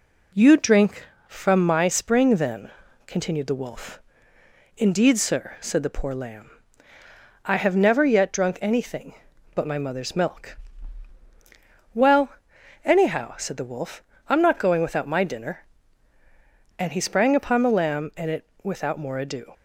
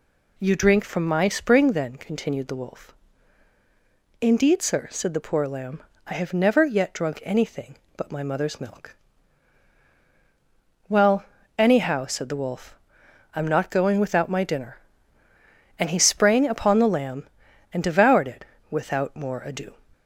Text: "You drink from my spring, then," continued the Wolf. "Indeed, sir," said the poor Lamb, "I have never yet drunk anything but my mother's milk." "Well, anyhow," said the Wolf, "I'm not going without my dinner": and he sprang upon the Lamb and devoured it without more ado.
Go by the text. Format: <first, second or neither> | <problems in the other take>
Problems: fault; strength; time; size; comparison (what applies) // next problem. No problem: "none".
second | skips "devoured"; at 18.3 s // pauses between "it" and "without"; slight; at 18.4 s; 0.16 s long; slight in the second